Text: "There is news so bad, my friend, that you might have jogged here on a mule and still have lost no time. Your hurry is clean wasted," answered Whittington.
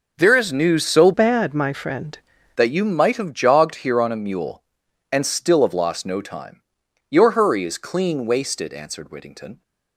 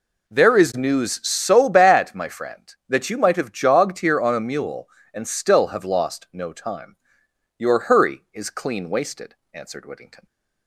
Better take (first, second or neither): second